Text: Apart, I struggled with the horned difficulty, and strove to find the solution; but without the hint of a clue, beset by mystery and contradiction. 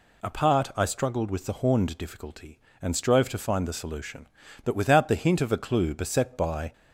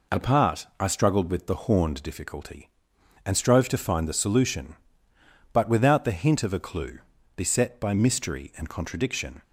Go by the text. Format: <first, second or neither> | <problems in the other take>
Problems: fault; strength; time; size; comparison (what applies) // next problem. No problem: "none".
second | stops before "mystery and contradiction"; at 6.7 s